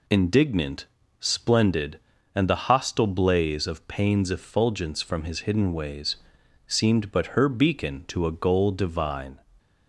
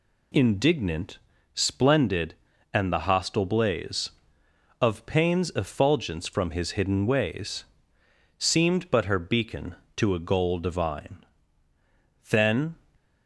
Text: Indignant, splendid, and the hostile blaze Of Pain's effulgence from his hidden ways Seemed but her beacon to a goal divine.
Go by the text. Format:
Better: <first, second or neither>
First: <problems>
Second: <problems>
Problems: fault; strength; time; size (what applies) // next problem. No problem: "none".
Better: first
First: pauses between "ways" and "Seemed"; noticeable; at 6.1 s; 0.50 s long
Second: pauses between "ways" and "Seemed"; noticeable; at 7.6 s; 0.74 s long // goes on to say "Then"; slight; from 12.3 s on; 0.46 s long